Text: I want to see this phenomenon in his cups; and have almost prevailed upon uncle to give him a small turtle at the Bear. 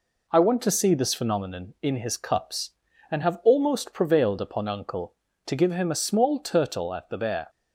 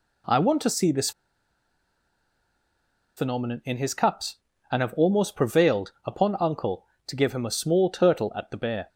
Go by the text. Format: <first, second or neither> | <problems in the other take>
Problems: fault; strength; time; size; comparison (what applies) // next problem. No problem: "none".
first | pauses between "this" and "phenomenon"; strong; at 1.1 s; 2.0 s long